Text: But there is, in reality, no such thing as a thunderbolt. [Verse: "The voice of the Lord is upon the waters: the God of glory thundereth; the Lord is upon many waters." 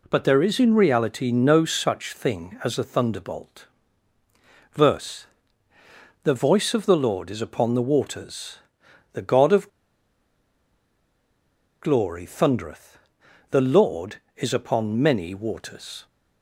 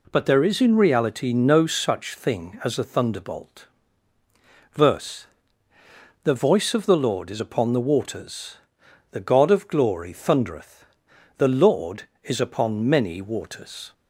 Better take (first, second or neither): second